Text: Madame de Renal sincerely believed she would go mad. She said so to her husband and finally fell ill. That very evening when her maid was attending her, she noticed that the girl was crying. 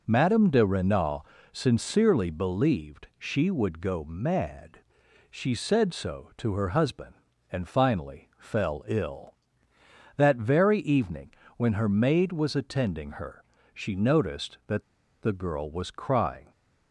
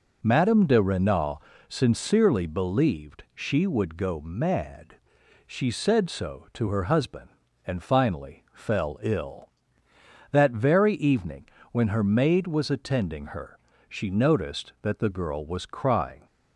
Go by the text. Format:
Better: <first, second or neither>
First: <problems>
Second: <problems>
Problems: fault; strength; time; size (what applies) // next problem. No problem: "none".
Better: second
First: pauses between "Renal" and "sincerely"; slight; at 1.2 s; 0.28 s long // pauses between "evening" and "when"; slight; at 11.3 s; 0.26 s long // pauses between "that" and "the"; at 14.8 s; 0.38 s long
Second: pauses between "Renal" and "sincerely"; slight; at 1.4 s; 0.28 s long // pauses between "evening" and "when"; slight; at 11.4 s; 0.26 s long